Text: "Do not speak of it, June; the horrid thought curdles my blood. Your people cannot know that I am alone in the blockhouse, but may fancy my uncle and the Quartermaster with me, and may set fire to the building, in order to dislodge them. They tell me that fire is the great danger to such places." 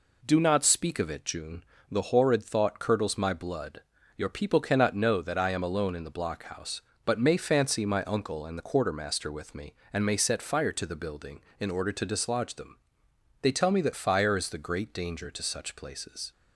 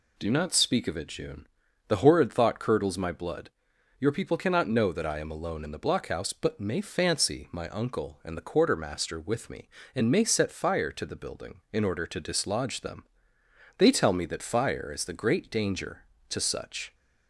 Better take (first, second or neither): first